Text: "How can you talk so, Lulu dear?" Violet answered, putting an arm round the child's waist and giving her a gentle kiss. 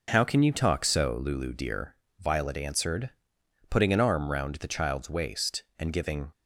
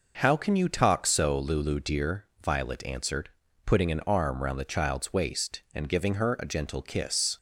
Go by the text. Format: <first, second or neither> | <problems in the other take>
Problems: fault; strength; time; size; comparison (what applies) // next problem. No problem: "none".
second | stops before "her a gentle kiss"; at 6.3 s